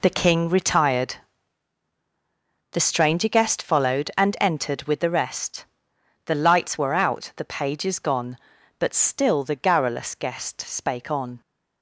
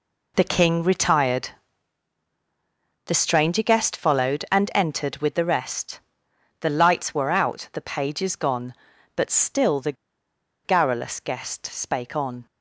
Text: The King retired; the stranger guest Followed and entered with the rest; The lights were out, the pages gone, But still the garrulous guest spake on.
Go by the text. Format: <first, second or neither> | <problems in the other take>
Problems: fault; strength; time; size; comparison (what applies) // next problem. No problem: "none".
first | pauses between "the" and "garrulous"; noticeable; at 9.9 s; 0.71 s long